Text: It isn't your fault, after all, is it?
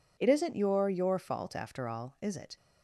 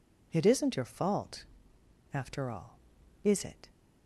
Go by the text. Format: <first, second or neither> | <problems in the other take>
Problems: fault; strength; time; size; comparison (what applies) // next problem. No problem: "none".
second | says "your" twice; at 0.8 s